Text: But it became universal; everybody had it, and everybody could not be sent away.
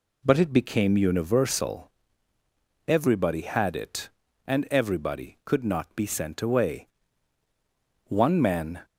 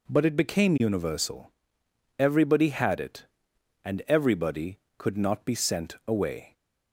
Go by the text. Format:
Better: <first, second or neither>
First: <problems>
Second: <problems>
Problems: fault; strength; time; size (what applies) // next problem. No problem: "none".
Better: second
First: goes on to say "One man"; noticeable; from 8.0 s on; 0.78 s long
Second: none